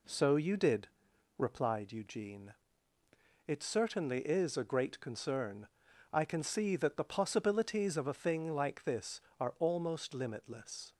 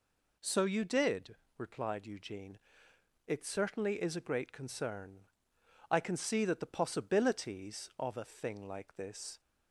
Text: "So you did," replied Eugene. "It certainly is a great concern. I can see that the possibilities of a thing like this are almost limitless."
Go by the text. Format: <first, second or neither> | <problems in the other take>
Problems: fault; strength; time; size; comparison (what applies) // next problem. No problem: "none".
first | stops before "are almost limitless"; at 9.4 s